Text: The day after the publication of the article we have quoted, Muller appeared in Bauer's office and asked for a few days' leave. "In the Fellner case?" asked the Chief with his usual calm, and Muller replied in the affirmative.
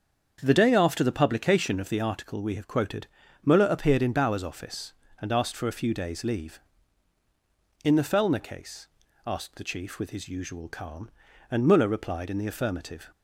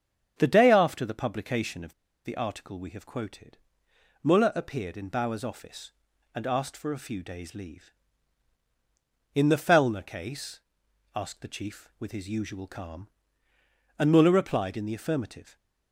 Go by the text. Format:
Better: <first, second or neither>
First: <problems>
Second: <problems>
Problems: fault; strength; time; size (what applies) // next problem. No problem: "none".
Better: first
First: starts louder than the rest; strong; until 1.4 s; 7 dB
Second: starts louder than the rest; strong; until 1.3 s; 7.5 dB // pauses between "of" and "the"; slight; at 1.9 s; 0.32 s long